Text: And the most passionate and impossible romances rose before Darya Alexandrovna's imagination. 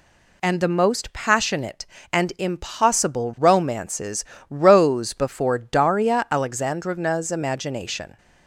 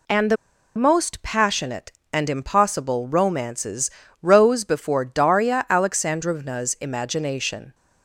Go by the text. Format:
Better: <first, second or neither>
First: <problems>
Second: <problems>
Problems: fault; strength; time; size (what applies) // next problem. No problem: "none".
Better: first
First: pauses between "romances" and "rose"; slight; at 4.2 s; 0.24 s long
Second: pauses between "the" and "most"; at 0.3 s; 0.40 s long // pauses between "romances" and "rose"; slight; at 3.8 s; 0.32 s long